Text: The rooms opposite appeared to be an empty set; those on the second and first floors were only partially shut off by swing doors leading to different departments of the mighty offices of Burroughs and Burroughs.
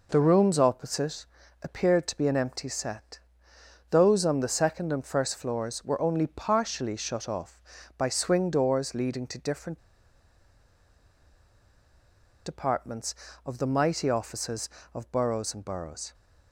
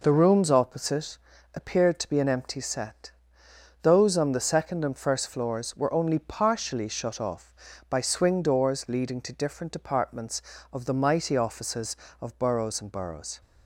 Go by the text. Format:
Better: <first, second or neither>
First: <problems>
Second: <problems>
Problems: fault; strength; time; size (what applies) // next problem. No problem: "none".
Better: second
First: pauses between "opposite" and "appeared"; at 1.2 s; 0.38 s long // pauses between "different" and "departments"; strong; at 9.7 s; 2.6 s long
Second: pauses between "opposite" and "appeared"; at 1.1 s; 0.38 s long